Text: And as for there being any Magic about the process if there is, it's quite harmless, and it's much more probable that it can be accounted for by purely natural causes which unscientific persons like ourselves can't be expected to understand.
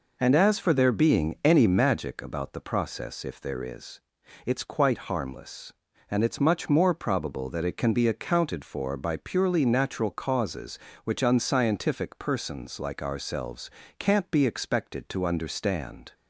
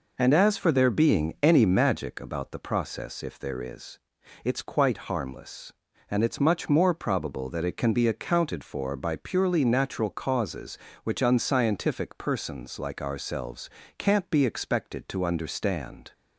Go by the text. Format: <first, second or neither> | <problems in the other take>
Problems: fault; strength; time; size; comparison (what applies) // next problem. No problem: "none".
neither | pauses between "ourselves" and "can't"; slight; the same in both